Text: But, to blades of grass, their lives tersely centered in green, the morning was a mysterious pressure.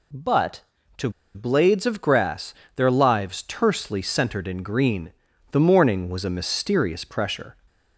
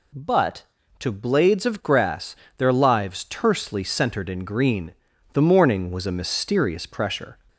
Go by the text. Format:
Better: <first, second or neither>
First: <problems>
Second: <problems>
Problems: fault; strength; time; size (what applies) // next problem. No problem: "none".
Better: second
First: pauses between "to" and "blades"; slight; at 1.0 s; 0.25 s long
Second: none